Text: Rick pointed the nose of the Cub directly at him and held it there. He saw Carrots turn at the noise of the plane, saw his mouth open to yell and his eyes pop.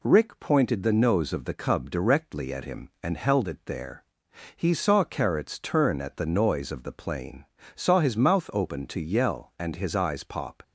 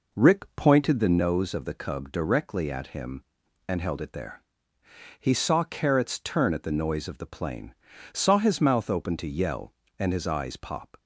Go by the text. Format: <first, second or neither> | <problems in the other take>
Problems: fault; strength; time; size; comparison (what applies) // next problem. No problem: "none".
first | starts louder than the rest; noticeable; until 1.3 s; 4.5 dB